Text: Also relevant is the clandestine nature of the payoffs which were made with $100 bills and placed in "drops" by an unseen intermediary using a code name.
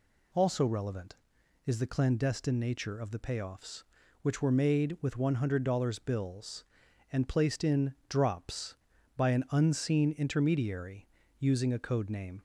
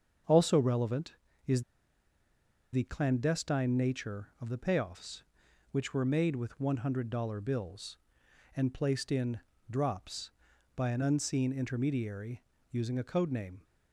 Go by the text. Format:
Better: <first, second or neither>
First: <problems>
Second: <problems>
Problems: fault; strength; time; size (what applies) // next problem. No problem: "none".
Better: first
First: pauses between "intermediary" and "using"; slight; at 11.0 s; 0.32 s long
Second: starts louder than the rest; strong; until 1.5 s; 7 dB // pauses between "is" and "the"; at 1.6 s; 1.1 s long // pauses between "in" and "drops"; slight; at 9.3 s; 0.28 s long // pauses between "intermediary" and "using"; slight; at 12.4 s; 0.28 s long